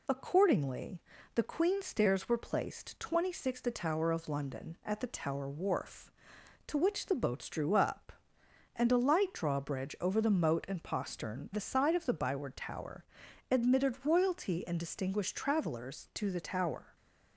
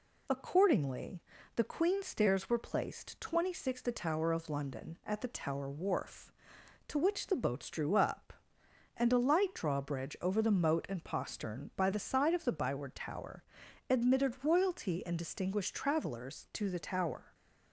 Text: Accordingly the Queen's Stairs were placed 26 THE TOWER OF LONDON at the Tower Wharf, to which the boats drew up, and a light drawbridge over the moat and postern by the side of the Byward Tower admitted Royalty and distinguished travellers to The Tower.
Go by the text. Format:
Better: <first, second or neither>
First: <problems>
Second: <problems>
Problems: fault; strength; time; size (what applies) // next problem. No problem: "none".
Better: second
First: pauses between "Accordingly" and "the"; slight; at 1.0 s; 0.36 s long // skips "by"; at 11.5 s // pauses between "Tower" and "admitted"; noticeable; at 13.0 s; 0.48 s long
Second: pauses between "Accordingly" and "the"; slight; at 1.2 s; 0.36 s long // pauses between "Tower" and "admitted"; noticeable; at 13.4 s; 0.48 s long